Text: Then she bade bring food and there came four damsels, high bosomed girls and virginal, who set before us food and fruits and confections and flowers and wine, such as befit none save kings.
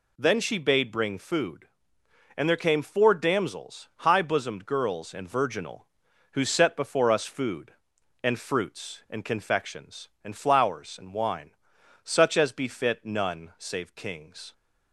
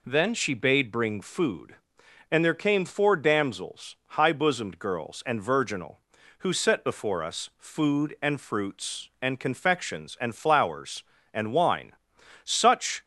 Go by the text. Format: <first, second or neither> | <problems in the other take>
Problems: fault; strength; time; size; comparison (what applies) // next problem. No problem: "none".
first | stops before "as befit none save kings"; at 13.0 s